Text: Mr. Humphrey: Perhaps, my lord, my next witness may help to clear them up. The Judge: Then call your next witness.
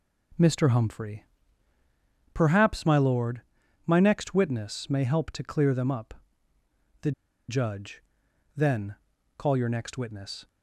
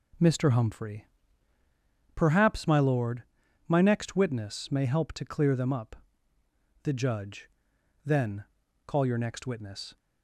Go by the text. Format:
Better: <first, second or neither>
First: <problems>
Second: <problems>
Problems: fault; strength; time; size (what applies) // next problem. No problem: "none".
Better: second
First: pauses between "The" and "Judge"; at 7.1 s; 0.37 s long // pauses between "Then" and "call"; at 8.9 s; 0.42 s long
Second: pauses between "Then" and "call"; at 8.4 s; 0.42 s long